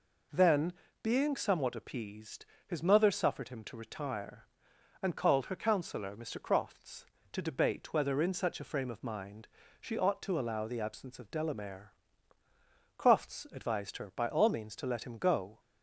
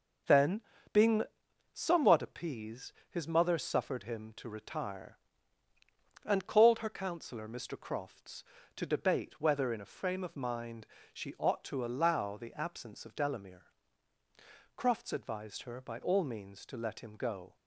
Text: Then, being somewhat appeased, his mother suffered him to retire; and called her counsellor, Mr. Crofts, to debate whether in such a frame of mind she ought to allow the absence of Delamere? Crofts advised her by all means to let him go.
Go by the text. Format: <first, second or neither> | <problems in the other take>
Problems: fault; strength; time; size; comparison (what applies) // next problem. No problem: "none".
first | pauses between "being" and "somewhat"; noticeable; at 1.2 s; 0.50 s long // skips "such"; at 9.8 s // pauses between "mind" and "she"; slight; at 10.8 s; 0.26 s long; slight in the first